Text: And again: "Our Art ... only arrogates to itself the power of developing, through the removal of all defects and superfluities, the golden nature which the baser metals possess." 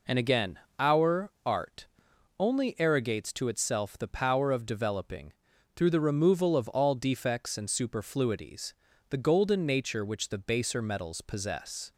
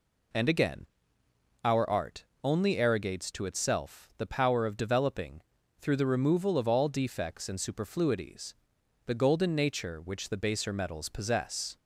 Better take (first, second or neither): neither